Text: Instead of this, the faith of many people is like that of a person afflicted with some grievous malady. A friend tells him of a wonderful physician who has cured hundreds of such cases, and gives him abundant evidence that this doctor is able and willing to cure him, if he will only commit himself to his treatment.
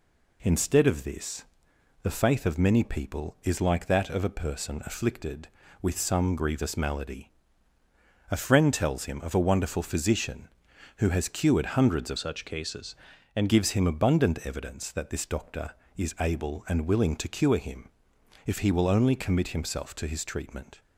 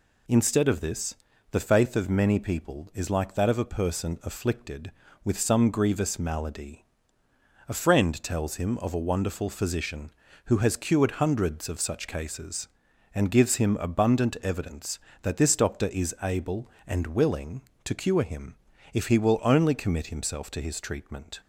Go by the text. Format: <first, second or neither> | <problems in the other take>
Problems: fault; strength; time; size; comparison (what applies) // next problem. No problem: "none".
second | changes voice from "such" to "and"; from 12.1 to 13.4 s; 1.3 s long